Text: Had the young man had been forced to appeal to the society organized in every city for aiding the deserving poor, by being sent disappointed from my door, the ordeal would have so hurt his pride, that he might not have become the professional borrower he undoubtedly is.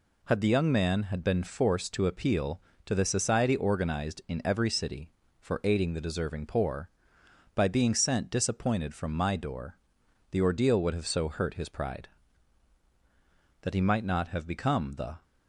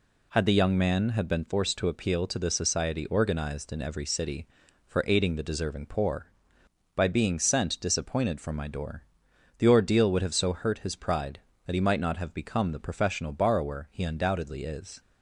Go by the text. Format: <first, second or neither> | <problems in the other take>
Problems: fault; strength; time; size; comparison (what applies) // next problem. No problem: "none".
second | stops before "professional borrower he undoubtedly is"; at 15.2 s